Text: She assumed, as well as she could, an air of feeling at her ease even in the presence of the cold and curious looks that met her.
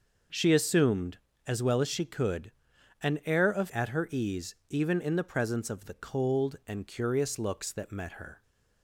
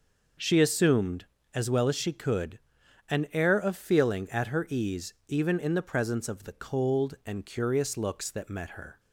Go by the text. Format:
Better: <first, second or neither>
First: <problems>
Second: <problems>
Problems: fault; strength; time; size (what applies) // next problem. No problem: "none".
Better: second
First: skips "feeling"; at 3.6 s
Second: none